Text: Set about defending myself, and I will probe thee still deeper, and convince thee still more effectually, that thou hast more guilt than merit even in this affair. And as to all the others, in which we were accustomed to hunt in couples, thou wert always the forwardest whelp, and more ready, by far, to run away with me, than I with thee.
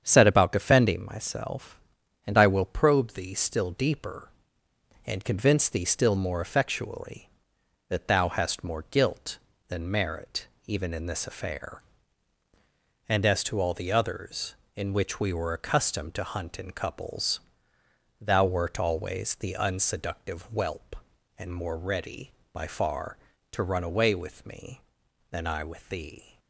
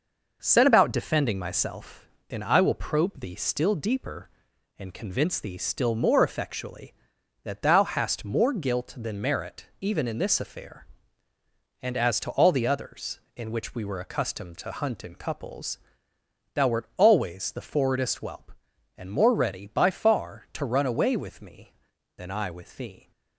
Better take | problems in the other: second | starts louder than the rest; strong; until 1.0 s; 8 dB // pauses between "merit" and "even"; slight; at 10.4 s; 0.20 s long // says "unseductive" for "forwardest"; at 19.5 s

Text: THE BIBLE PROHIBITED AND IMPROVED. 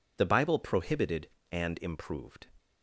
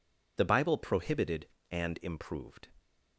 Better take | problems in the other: neither | none

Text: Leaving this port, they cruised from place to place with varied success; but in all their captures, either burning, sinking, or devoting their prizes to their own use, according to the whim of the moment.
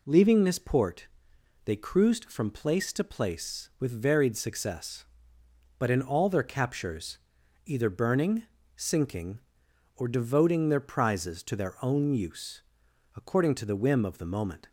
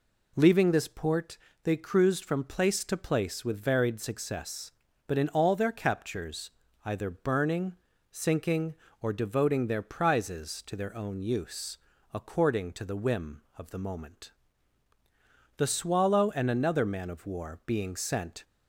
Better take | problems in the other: first | goes on to say "The Swallow and another man of war being sent"; strong; from 15.5 s on; 2.8 s long

